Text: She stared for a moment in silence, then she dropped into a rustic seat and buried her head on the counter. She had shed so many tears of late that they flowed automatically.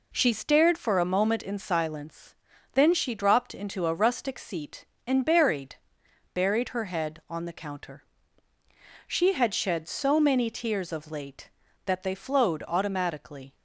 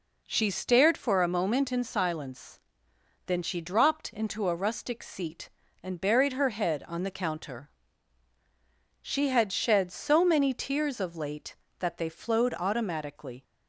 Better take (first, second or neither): second